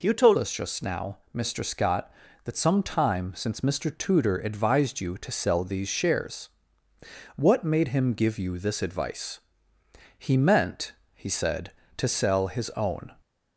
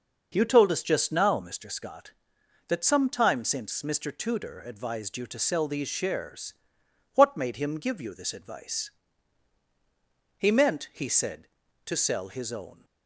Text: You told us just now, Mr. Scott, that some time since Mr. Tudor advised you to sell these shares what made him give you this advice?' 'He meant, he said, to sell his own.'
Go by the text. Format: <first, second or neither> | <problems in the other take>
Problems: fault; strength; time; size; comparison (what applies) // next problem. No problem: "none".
second | changes voice at "us"; from 0.3 s on; 12.8 s long // pauses between "shares" and "what"; noticeable; at 6.4 s; 0.86 s long; noticeable in the second